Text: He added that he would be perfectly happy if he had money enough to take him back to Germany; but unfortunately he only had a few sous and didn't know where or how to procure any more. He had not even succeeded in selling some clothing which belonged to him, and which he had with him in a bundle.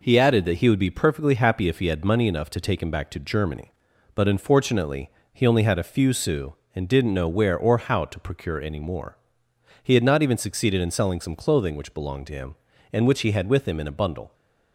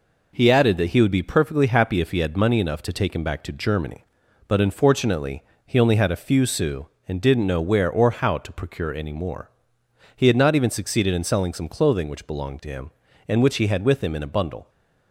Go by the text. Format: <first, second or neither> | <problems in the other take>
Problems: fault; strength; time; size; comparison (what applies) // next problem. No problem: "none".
neither | pauses between "unfortunately" and "he"; slight; the same in both